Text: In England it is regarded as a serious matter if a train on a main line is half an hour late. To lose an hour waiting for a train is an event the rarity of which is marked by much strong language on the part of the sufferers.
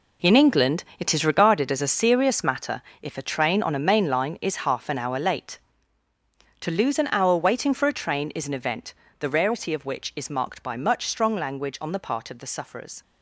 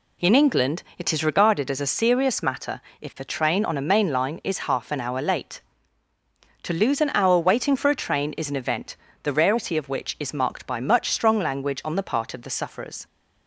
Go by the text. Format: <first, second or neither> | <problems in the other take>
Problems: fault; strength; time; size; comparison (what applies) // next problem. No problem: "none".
second | gets quieter; strong; throughout; 10.5 dB // pauses between "England" and "it"; slight; at 0.8 s; 0.16 s long; slight in the second // pauses between "matter" and "if"; slight; at 2.8 s; 0.18 s long; slight in the second // pauses between "event" and "the"; slight; at 8.9 s; 0.26 s long; slight in the second